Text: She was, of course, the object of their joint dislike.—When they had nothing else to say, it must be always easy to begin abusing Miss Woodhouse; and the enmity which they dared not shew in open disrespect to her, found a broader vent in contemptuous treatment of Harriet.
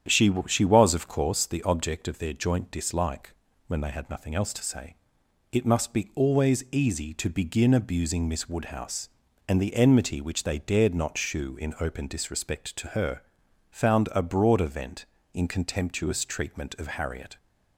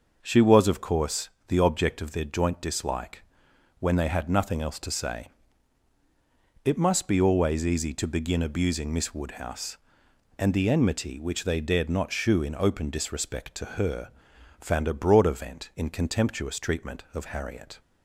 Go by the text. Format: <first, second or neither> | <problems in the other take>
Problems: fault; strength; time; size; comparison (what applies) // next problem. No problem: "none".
second | starts louder than the rest; strong; until 1.2 s; 9 dB // says "She" twice; at 0.4 s